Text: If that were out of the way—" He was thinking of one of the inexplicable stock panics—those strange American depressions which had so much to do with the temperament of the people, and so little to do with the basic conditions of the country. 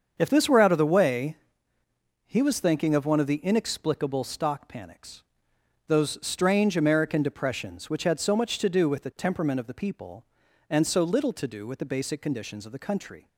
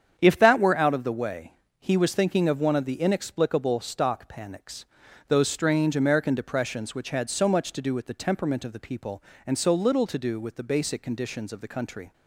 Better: second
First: starts louder than the rest; until 1.1 s; 7 dB // says "this" for "that"; at 0.2 s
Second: starts louder than the rest; strong; until 1.2 s; 8 dB

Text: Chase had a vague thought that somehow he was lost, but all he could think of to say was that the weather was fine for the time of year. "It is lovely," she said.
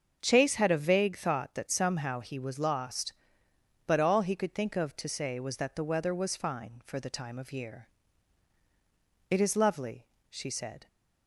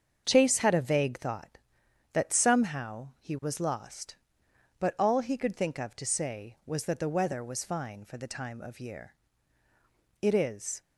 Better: first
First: starts louder than the rest; until 1.2 s; 7 dB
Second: starts louder than the rest; strong; until 1.2 s; 7 dB // stops before "lovely she said"; at 10.8 s

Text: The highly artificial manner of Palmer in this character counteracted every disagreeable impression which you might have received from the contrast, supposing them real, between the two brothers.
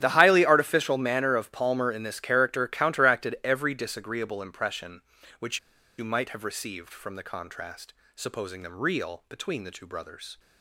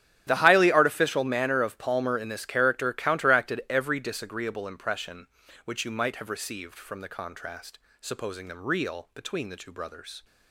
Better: second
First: starts louder than the rest; strong; until 1.0 s; 10 dB // pauses between "which" and "you"; at 5.5 s; 0.39 s long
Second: starts louder than the rest; strong; until 1.2 s; 10.5 dB

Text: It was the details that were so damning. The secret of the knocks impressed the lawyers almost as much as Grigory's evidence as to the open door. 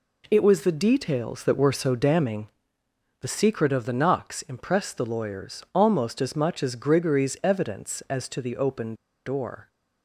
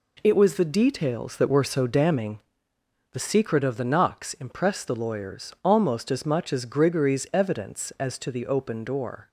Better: second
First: pauses between "open" and "door"; slight; at 8.9 s; 0.31 s long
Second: none

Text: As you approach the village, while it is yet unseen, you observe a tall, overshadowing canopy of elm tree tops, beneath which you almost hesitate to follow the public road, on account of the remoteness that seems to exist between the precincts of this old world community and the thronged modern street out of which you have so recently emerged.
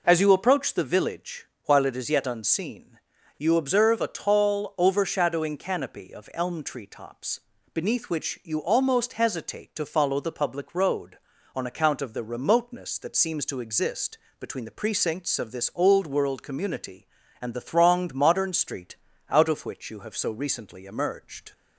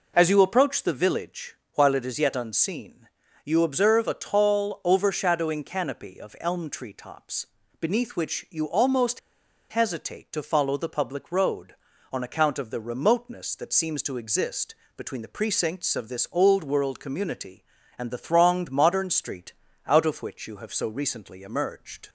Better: first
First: pauses between "exist" and "between"; slight; at 14.1 s; 0.24 s long // pauses between "street" and "out"; slight; at 18.9 s; 0.32 s long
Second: pauses between "almost" and "hesitate"; noticeable; at 9.1 s; 0.51 s long // pauses between "exist" and "between"; slight; at 14.7 s; 0.24 s long // pauses between "street" and "out"; slight; at 19.5 s; 0.32 s long

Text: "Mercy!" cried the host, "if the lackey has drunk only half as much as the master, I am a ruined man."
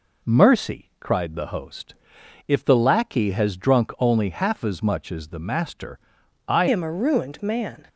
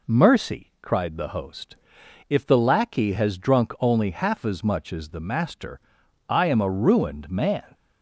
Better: second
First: changes voice at "am"; from 6.6 s on; 1.2 s long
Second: none

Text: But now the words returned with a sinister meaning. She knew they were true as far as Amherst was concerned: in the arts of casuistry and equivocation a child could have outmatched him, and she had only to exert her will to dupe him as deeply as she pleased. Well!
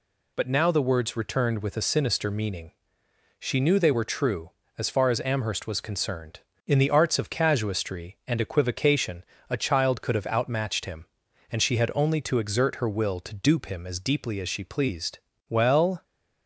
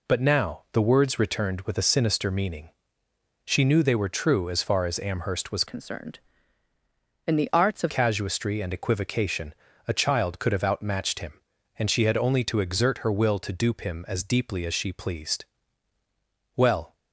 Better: first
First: pauses between "equivocation" and "a"; slight; at 9.2 s; 0.26 s long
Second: changes voice from "concerned" to "of"; from 5.6 to 7.9 s; 2.3 s long // pauses between "equivocation" and "a"; slight; at 9.5 s; 0.34 s long

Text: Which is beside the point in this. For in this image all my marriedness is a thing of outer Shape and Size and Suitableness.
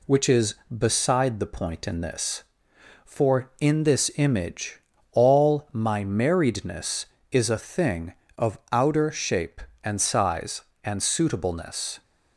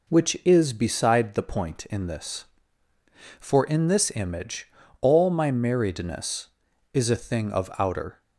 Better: first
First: pauses between "image" and "all"; slight; at 4.7 s; 0.32 s long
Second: pauses between "image" and "all"; slight; at 4.6 s; 0.32 s long // stops before "Shape and Size and Suitableness"; at 8.2 s

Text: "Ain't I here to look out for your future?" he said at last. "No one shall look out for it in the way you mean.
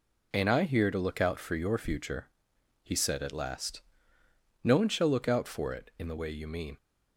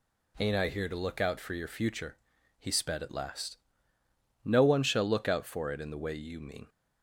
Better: first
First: none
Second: says "sped" for "said"; at 2.7 s

